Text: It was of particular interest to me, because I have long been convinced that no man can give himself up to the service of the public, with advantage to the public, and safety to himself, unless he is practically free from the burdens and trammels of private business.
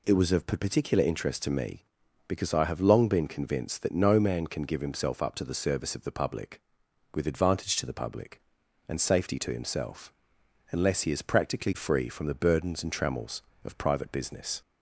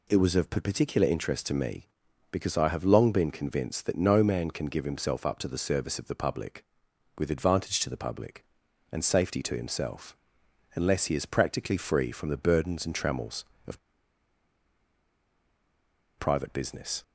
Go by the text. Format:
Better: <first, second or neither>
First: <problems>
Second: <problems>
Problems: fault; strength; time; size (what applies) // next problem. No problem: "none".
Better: first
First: none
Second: pauses between "of" and "private"; strong; at 13.7 s; 2.4 s long